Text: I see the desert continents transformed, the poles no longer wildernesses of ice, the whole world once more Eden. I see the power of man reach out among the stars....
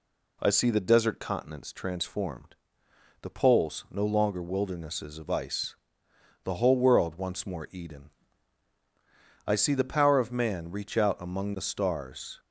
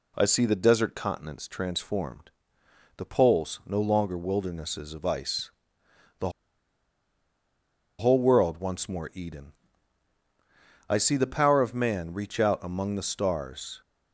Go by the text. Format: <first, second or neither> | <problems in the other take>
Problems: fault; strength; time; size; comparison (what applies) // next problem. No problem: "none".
first | pauses between "the" and "whole"; strong; at 6.2 s; 1.6 s long